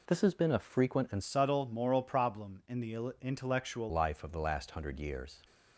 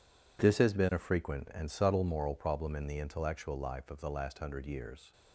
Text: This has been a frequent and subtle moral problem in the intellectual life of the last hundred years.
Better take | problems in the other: second | changes voice from "subtle" to "intellectual"; from 1.2 to 3.9 s; 2.7 s long

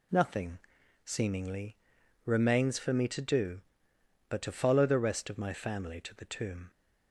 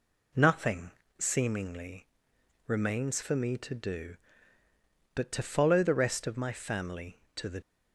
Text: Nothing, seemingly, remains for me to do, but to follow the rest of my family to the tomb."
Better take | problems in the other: first | stops before "tomb"; at 7.6 s

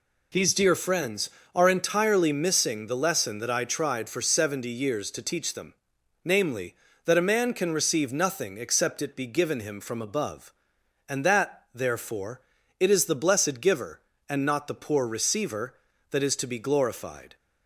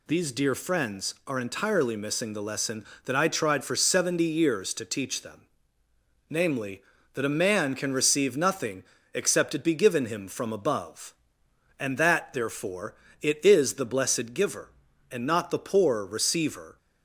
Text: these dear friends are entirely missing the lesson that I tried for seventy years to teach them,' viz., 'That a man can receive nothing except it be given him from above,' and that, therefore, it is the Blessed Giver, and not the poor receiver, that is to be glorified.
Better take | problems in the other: first | pauses between "nothing" and "except"; slight; at 8.8 s; 0.28 s long // stops before "that is to be glorified"; at 16.7 s

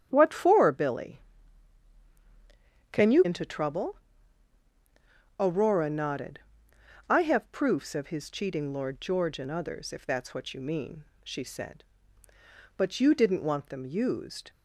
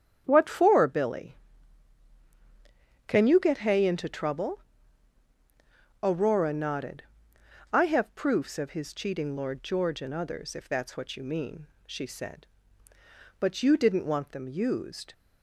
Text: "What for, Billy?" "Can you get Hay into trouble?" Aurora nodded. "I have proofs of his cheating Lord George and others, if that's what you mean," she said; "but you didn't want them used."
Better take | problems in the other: second | starts louder than the rest; strong; until 1.1 s; 9.5 dB; strong in the second // skips "get Hay"; at 3.2 s

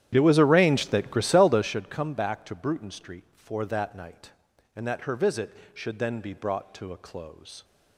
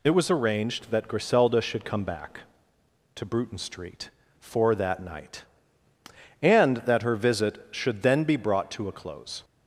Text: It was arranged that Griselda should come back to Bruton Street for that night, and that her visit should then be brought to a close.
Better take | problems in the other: second | starts louder than the rest; strong; until 1.8 s; 11 dB

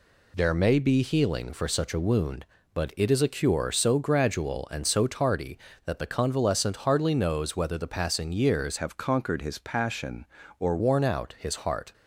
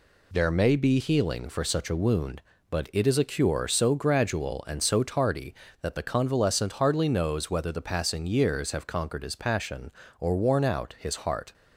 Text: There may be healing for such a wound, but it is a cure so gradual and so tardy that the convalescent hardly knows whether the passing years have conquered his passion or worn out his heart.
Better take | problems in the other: second | changes voice from "have" to "or"; from 8.7 to 10.7 s; 2.0 s long

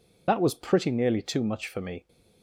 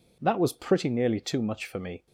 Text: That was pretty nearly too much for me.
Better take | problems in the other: second | loses the start of "That"; at 0.2 s; 65 ms

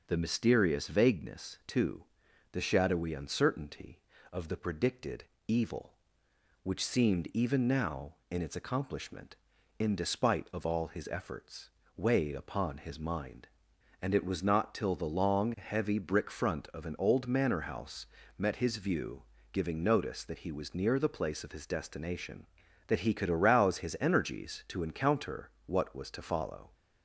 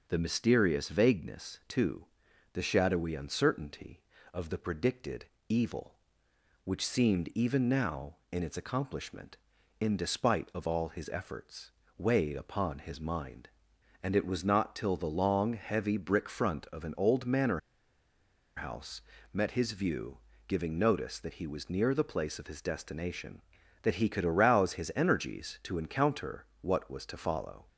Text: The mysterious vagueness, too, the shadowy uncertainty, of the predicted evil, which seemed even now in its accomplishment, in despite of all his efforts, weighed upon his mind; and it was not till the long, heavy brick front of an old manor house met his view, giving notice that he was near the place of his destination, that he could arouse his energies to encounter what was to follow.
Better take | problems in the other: first | pauses between "predicted" and "evil"; slight; at 5.2 s; 0.24 s long; slight in the first // pauses between "manor" and "house"; noticeable; at 17.5 s; 0.97 s long // pauses between "house" and "met"; slight; at 19.0 s; 0.32 s long; slight in the first // pauses between "encounter" and "what"; slight; at 26.4 s; 0.16 s long; slight in the first

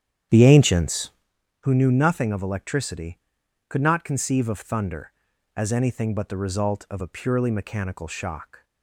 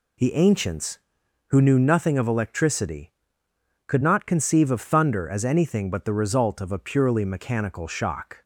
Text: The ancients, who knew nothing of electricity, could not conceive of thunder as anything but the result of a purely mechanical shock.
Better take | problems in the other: second | starts louder than the rest; strong; until 1.3 s; 9.5 dB

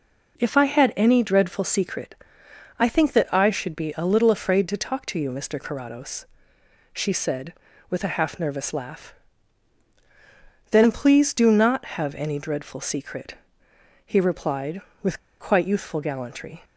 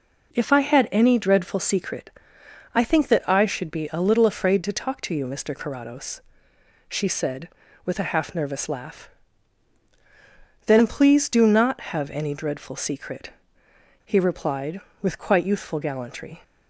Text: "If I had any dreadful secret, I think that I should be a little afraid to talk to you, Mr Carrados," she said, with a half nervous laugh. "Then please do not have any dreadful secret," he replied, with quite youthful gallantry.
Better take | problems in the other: second | pauses between "with" and "quite"; slight; at 15.1 s; 0.20 s long

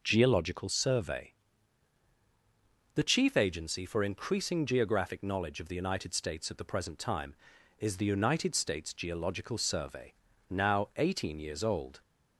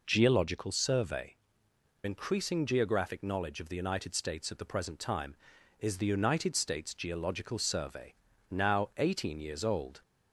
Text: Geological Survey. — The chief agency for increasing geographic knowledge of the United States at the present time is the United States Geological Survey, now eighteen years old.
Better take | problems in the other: first | skips "The chief agency for"; at 1.7 s

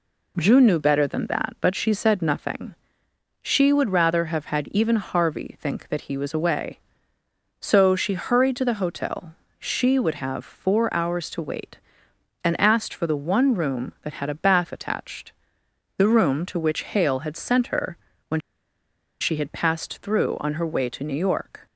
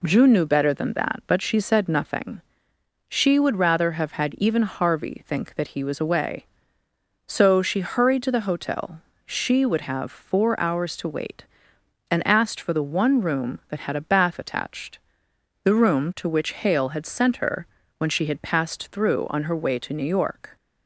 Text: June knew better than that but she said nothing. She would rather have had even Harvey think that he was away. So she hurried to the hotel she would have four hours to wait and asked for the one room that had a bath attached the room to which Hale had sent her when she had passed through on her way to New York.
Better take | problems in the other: second | pauses between "hotel" and "she"; slight; at 9.3 s; 0.24 s long; slight in the second // pauses between "attached" and "the"; noticeable; at 15.3 s; 0.64 s long; noticeable in the second // pauses between "her" and "when"; slight; at 17.9 s; 0.32 s long; slight in the second // pauses between "when" and "she"; noticeable; at 18.3 s; 0.80 s long

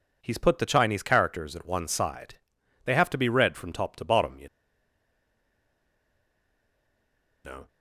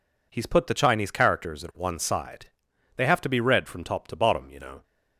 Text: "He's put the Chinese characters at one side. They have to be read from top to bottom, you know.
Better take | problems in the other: second | pauses between "you" and "know"; strong; at 4.4 s; 2.9 s long

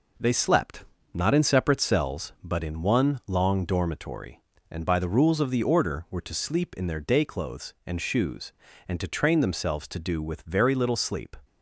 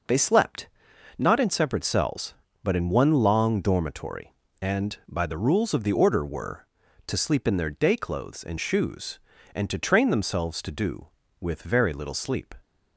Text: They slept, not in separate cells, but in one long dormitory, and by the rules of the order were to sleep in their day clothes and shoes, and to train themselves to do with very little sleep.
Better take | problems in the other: neither | none

